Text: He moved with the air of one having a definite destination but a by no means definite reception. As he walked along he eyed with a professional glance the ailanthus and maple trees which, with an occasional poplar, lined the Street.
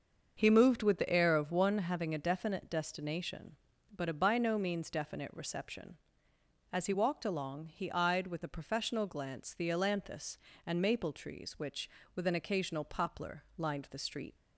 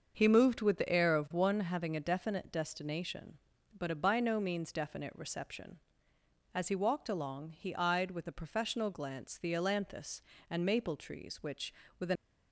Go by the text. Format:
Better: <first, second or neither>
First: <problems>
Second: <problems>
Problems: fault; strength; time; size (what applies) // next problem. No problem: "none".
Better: first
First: starts louder than the rest; until 1.3 s; 6.5 dB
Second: starts louder than the rest; until 1.1 s; 6.5 dB // stops before "occasional poplar lined the Street"; at 12.1 s